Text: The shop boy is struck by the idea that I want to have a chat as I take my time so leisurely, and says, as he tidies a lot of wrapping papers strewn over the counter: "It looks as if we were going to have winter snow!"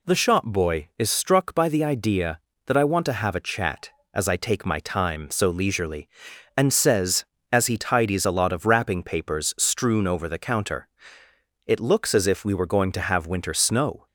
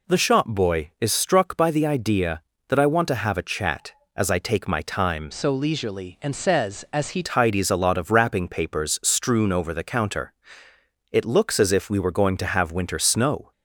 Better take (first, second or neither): first